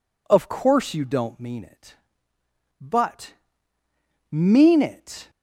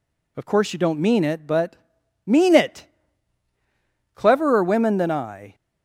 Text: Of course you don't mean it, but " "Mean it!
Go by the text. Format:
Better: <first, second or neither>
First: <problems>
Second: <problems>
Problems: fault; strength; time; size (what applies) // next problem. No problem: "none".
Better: first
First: none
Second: goes on to say "Cleverer women than I"; from 4.1 s on; 1.3 s long